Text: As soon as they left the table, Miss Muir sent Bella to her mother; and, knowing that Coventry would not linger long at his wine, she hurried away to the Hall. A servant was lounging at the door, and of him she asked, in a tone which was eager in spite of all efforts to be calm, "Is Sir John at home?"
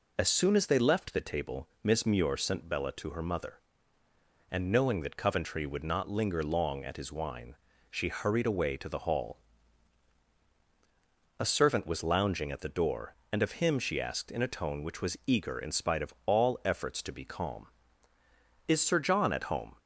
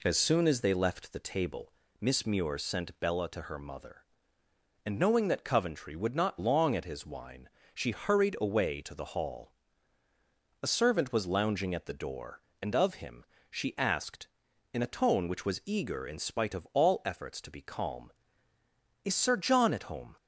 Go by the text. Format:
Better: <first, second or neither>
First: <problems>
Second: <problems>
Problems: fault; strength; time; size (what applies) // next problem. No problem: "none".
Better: first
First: none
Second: skips "linger"; at 6.3 s // pauses between "him" and "she"; slight; at 13.2 s; 0.24 s long